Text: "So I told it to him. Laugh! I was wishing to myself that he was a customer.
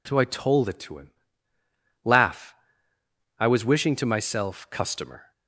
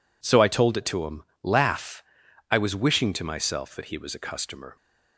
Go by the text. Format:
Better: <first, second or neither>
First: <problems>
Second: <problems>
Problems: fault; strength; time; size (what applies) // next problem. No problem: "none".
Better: second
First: skips "that he was a"; at 4.7 s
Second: none